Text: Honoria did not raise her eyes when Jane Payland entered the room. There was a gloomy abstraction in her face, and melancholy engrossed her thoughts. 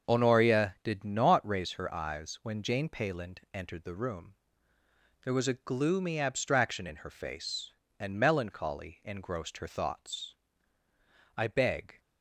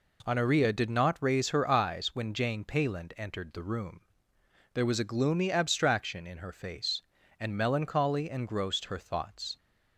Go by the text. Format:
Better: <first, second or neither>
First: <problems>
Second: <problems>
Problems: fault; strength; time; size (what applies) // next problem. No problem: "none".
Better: second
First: starts louder than the rest; until 1.1 s; 6.5 dB // pauses between "Payland" and "entered"; slight; at 3.3 s; 0.16 s long // goes on to say "I beg"; noticeable; from 11.3 s on; 0.62 s long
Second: none